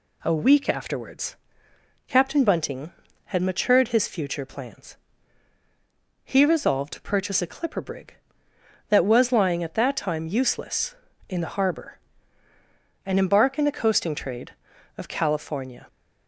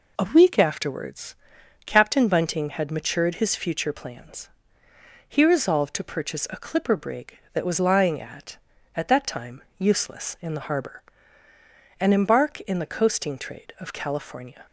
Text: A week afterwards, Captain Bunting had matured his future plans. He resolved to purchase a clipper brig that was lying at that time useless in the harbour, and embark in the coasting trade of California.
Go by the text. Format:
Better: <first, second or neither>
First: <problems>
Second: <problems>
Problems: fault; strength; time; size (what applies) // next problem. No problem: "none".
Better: first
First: none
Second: says "at" twice; at 8.9 s // pauses between "time" and "useless"; slight; at 9.6 s; 0.16 s long